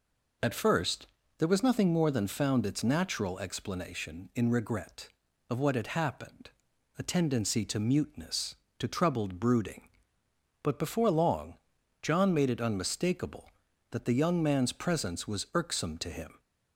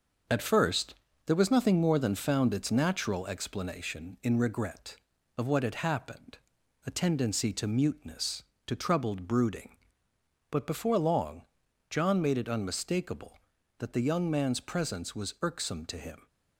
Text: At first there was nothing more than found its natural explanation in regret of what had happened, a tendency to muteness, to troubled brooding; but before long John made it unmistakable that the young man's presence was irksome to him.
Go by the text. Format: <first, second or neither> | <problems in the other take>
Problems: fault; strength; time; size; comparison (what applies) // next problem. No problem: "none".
first | gets quieter; throughout; 6.5 dB // pauses between "first" and "there"; slight; at 0.9 s; 0.32 s long; slight in the first // pauses between "long" and "John"; at 11.4 s; 0.44 s long; also in the first